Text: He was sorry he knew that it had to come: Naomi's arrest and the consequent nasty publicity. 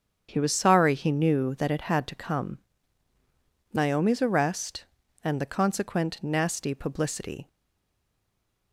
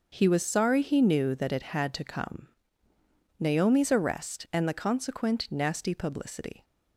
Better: second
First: starts louder than the rest; strong; until 1.3 s; 7.5 dB // stays silent after the last word; noticeable; from 7.4 s on; 1.3 s long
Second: starts louder than the rest; noticeable; until 1.1 s; 6 dB

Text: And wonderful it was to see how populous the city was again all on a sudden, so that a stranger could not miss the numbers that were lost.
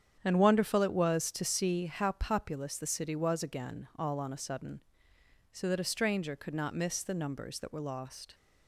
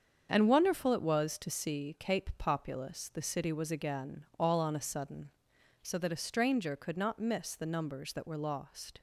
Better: first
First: starts louder than the rest; strong; until 1.2 s; 8.5 dB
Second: starts louder than the rest; strong; until 1.3 s; 7.5 dB // says "cape" for "how"; at 1.9 s

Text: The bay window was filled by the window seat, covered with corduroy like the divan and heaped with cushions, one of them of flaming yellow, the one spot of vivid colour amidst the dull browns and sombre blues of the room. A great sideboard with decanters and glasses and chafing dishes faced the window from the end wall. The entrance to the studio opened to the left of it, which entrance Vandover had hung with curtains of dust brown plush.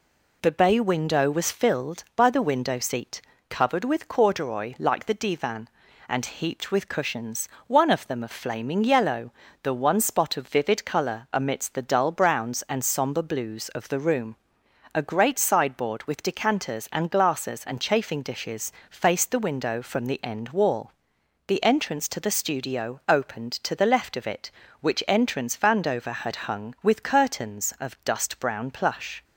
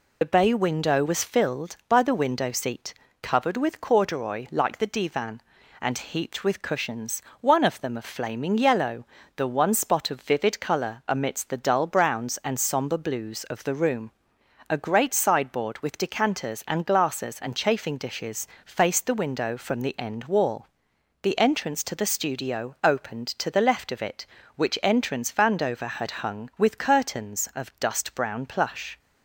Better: first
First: pauses between "dishes" and "faced"; slight; at 18.7 s; 0.20 s long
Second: loses the start of "The"; at 0.2 s; 50 ms // pauses between "dishes" and "faced"; slight; at 18.4 s; 0.20 s long

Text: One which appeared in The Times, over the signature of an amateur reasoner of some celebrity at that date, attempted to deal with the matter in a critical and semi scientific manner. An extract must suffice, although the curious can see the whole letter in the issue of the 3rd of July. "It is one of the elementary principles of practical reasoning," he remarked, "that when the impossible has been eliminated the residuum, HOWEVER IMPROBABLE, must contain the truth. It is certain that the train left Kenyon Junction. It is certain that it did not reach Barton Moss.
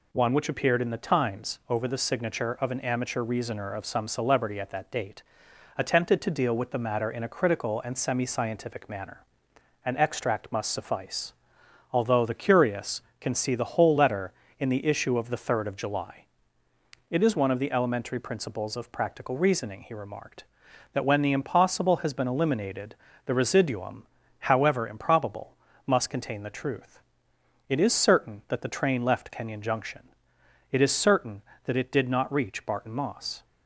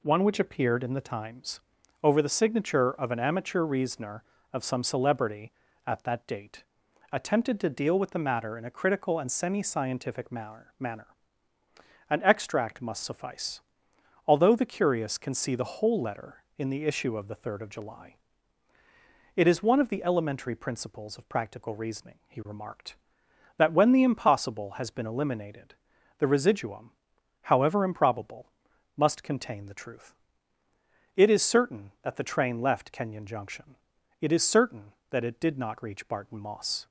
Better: first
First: pauses between "eliminated" and "the"; slight; at 22.9 s; 0.30 s long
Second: says "manner" twice; at 10.8 s // pauses between "eliminated" and "the"; at 25.7 s; 0.42 s long

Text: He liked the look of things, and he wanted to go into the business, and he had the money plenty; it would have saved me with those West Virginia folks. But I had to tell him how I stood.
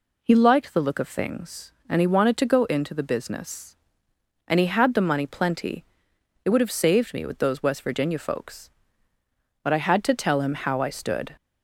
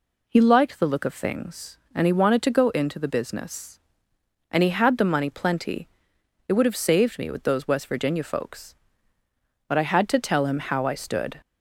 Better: neither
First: none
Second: none

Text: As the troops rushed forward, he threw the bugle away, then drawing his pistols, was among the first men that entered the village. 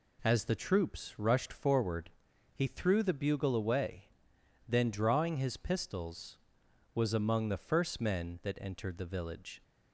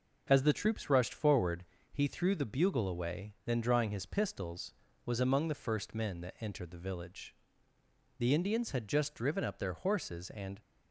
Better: first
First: none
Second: goes on to say "The Indians had just driven up their horses and"; strong; from 8.1 s on; 2.4 s long

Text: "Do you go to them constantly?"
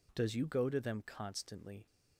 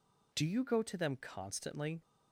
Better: second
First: says "Does" for "Do"; at 0.1 s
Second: none

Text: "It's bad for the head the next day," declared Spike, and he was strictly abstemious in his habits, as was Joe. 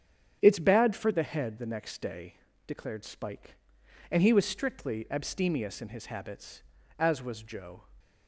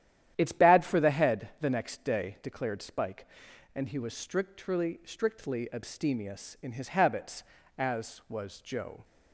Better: first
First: starts louder than the rest; strong; until 1.4 s; 7.5 dB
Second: starts louder than the rest; strong; until 1.3 s; 11 dB // says "strictly" twice; at 5.0 s

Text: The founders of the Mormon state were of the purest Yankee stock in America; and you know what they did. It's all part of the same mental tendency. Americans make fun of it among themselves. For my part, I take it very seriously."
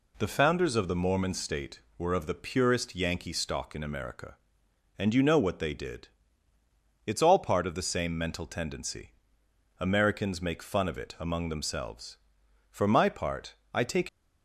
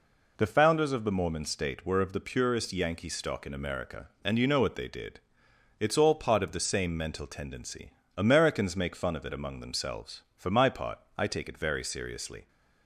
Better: second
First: stops before "it very seriously"; at 14.0 s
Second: none

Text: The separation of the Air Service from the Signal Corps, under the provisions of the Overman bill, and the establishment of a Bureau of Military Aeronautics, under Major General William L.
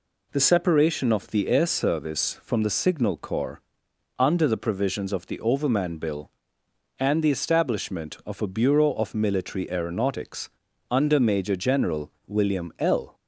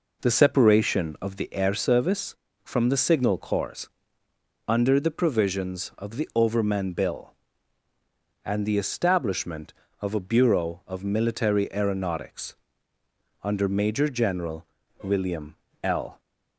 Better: first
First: pauses between "General" and "William"; slight; at 12.1 s; 0.16 s long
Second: starts louder than the rest; noticeable; until 1.5 s; 4.5 dB // pauses between "General" and "William"; slight; at 14.6 s; 0.36 s long // pauses between "William" and "L"; slight; at 15.5 s; 0.30 s long

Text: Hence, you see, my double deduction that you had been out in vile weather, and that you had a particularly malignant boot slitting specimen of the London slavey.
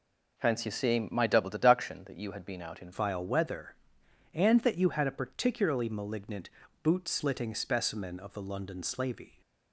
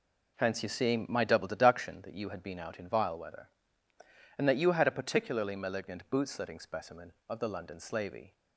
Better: second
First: changes voice at "vile"; from 2.9 s on; 6.5 s long // pauses between "malignant" and "boot"; slight; at 6.4 s; 0.34 s long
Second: none

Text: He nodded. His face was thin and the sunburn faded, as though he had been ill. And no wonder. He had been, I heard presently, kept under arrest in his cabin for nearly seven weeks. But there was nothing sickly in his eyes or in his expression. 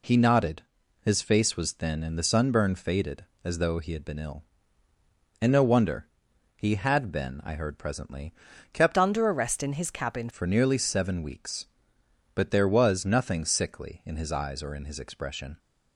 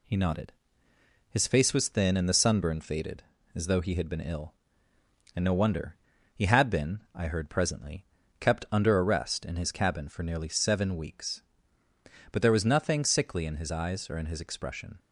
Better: second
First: changes voice from "under" to "cabin"; from 8.9 to 10.2 s; 1.3 s long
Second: none

